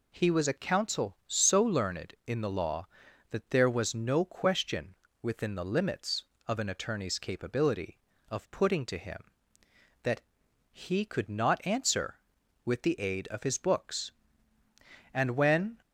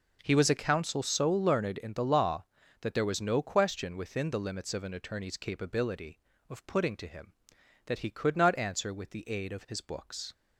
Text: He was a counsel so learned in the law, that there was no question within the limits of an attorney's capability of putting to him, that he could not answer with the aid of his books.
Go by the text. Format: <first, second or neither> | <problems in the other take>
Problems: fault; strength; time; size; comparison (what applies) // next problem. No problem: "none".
second | pauses between "question" and "within"; slight; at 4.9 s; 0.28 s long // pauses between "that" and "he"; noticeable; at 10.1 s; 0.54 s long // goes on to say "And when"; noticeable; from 15.1 s on; 0.64 s long